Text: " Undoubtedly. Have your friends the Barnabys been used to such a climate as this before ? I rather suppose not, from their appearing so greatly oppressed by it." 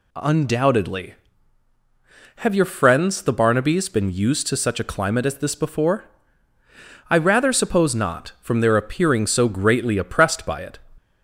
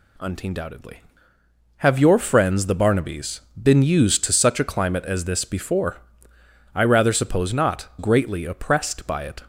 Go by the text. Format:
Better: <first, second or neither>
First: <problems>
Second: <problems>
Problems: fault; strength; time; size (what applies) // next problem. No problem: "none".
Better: first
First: none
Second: pauses between "Barnabys" and "been"; slight; at 3.4 s; 0.20 s long // skips "from their appearing so"; at 7.9 s